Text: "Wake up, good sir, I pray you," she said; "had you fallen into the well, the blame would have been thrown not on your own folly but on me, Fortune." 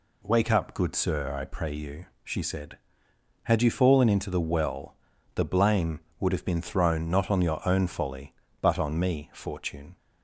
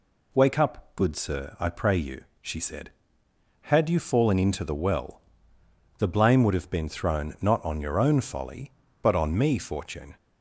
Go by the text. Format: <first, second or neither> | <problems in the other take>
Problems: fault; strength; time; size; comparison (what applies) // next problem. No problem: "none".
neither | none